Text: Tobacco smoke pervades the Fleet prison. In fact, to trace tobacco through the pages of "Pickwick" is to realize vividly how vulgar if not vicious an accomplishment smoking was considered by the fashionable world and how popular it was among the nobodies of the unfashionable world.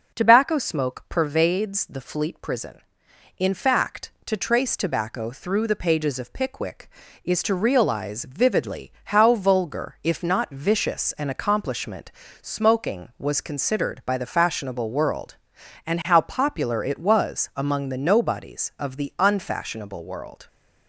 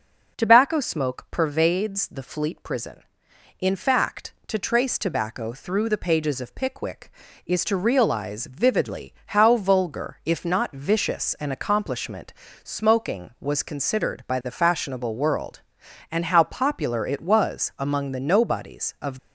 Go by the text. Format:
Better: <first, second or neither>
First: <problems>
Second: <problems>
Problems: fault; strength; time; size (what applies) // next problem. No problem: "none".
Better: first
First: pauses between "accomplishment" and "smoking"; slight; at 12.1 s; 0.32 s long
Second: pauses between "accomplishment" and "smoking"; slight; at 12.3 s; 0.32 s long // stops before "the unfashionable world"; at 19.1 s